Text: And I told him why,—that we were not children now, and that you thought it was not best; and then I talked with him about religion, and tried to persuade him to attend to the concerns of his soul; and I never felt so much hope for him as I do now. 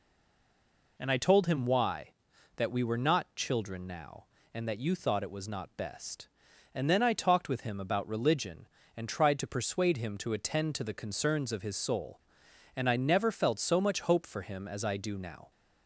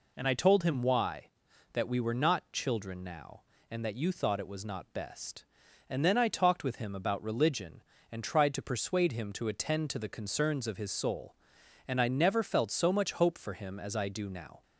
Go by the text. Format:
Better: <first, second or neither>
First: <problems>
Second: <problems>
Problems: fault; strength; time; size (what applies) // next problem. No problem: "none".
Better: second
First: stays silent before the first word; until 0.9 s; 0.9 s long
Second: none